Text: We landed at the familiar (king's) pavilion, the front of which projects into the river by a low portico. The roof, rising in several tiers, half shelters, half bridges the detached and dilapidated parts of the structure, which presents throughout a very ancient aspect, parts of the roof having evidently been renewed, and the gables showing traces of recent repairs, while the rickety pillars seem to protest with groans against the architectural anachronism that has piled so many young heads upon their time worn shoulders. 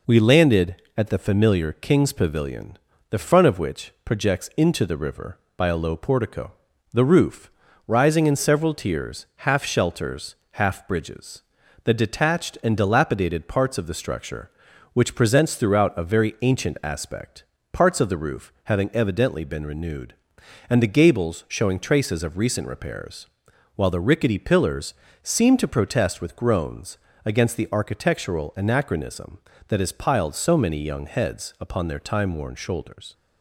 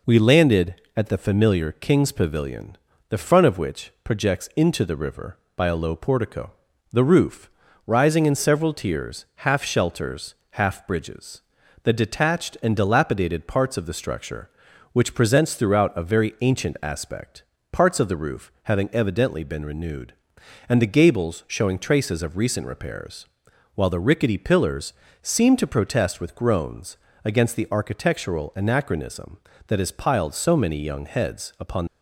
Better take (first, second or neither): first